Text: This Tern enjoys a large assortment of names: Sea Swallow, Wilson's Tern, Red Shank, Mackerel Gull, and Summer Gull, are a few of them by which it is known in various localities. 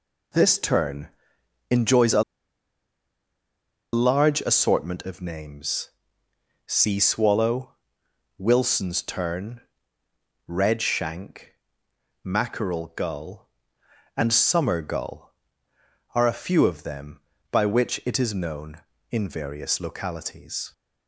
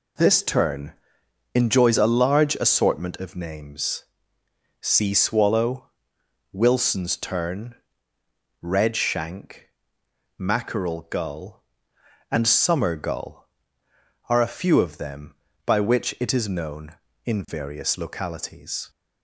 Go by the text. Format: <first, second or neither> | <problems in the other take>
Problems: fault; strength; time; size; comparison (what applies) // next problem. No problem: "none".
second | pauses between "Tern" and "enjoys"; noticeable; at 1.0 s; 0.60 s long; noticeable in the second // pauses between "a" and "large"; strong; at 2.2 s; 1.7 s long